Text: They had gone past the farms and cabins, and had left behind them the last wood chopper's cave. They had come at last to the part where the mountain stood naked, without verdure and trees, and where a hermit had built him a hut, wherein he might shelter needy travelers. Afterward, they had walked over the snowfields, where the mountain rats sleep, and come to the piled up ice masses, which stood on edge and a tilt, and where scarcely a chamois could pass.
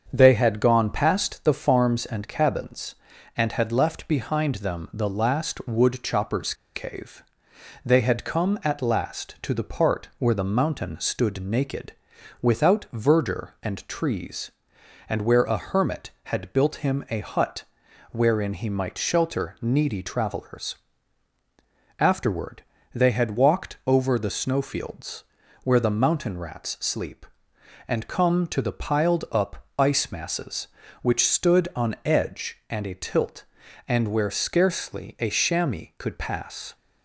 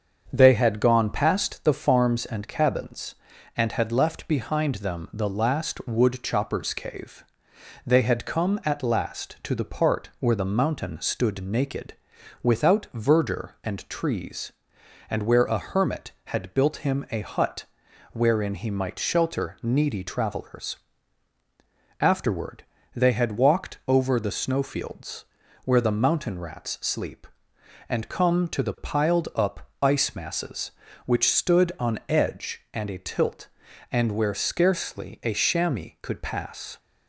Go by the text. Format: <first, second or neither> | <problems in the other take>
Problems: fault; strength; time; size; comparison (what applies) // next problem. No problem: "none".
second | starts louder than the rest; until 1.1 s; 7 dB; also in the second // pauses between "chopper's" and "cave"; slight; at 6.5 s; 0.21 s long // pauses between "up" and "ice"; slight; at 29.6 s; 0.16 s long; slight in the second